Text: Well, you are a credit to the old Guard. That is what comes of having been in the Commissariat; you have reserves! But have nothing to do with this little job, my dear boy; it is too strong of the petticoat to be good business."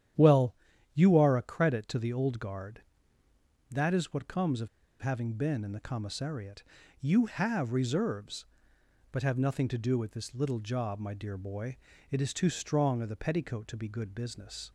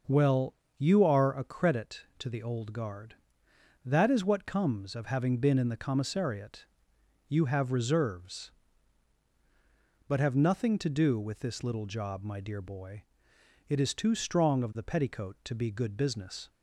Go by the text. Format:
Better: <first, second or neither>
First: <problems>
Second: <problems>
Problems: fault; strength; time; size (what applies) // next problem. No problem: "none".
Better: second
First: starts louder than the rest; strong; until 1.5 s; 10 dB // pauses between "of" and "having"; slight; at 4.6 s; 0.32 s long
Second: starts louder than the rest; until 1.3 s; 6 dB